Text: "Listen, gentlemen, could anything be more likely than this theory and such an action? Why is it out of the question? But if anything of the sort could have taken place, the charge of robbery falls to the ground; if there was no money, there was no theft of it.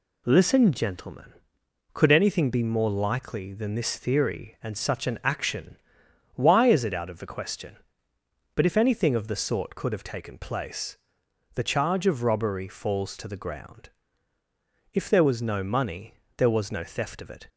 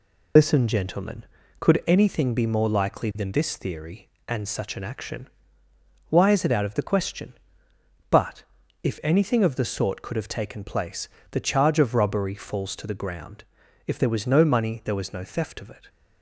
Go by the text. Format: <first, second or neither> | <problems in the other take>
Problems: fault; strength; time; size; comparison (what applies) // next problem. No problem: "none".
first | loses the start of "Listen"; at 0.3 s; 75 ms // pauses between "But" and "if"; at 8.4 s; 0.40 s long